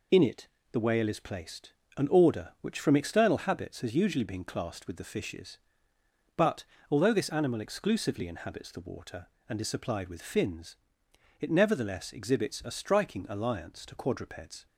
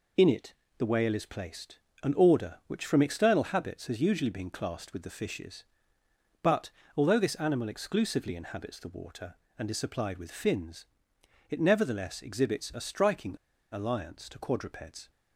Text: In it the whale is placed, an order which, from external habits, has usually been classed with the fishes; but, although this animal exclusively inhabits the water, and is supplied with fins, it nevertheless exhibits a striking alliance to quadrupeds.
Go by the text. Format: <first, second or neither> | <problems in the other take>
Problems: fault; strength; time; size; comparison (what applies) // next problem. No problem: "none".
first | pauses between "it" and "the"; slight; at 0.5 s; 0.24 s long; slight in the first // pauses between "striking" and "alliance"; slight; at 13.3 s; 0.35 s long